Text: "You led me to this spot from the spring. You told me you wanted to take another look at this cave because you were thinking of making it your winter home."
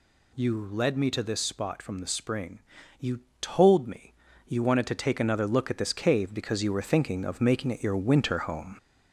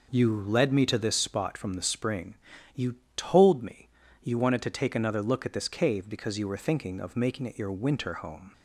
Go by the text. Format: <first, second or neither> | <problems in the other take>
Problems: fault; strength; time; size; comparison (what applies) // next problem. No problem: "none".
second | gets louder; throughout; 3.5 dB // pauses between "You" and "told"; slight; at 3.1 s; 0.20 s long; slight in the second // pauses between "me" and "you"; slight; at 4.1 s; 0.34 s long; slight in the second